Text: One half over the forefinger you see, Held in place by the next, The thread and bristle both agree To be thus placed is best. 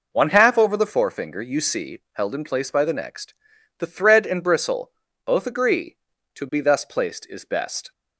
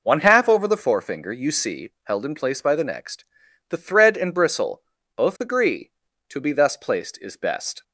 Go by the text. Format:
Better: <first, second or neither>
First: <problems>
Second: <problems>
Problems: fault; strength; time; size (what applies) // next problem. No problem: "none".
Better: neither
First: pauses between "bristle" and "both"; slight; at 4.9 s; 0.34 s long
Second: pauses between "bristle" and "both"; slight; at 4.8 s; 0.34 s long